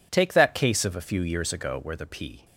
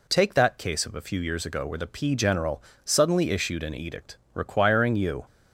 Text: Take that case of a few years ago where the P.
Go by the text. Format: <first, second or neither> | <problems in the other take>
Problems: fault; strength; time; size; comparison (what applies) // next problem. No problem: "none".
first | goes on to say "General suddenly issued an edict requiring you"; strong; from 2.1 s on; 3.1 s long